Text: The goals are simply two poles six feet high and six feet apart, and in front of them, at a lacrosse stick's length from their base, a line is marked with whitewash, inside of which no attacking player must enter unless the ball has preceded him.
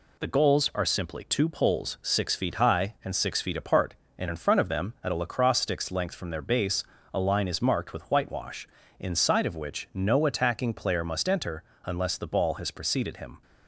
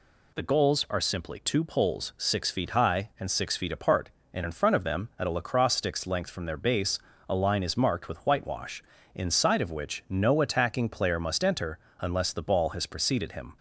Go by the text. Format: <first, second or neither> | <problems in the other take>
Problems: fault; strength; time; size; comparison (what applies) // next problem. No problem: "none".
second | gets quieter; throughout; 4 dB // pauses between "enter" and "unless"; slight; at 11.6 s; 0.20 s long; slight in the second